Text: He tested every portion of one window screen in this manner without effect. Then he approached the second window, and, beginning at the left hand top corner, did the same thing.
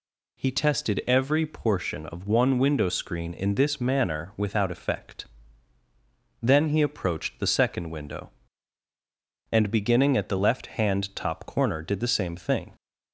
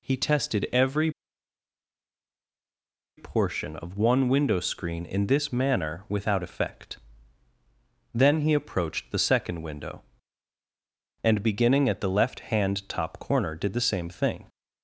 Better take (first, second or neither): first